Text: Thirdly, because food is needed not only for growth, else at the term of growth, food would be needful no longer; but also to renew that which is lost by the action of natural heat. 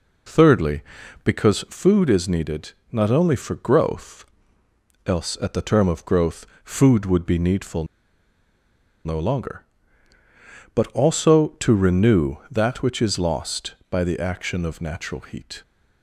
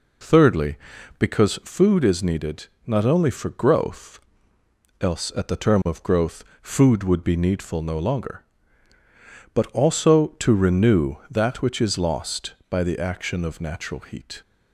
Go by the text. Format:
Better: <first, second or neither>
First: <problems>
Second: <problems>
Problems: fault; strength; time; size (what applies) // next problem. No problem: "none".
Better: second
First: pauses between "needed" and "not"; slight; at 2.7 s; 0.18 s long // pauses between "needful" and "no"; at 7.8 s; 1.1 s long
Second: pauses between "needed" and "not"; slight; at 2.6 s; 0.18 s long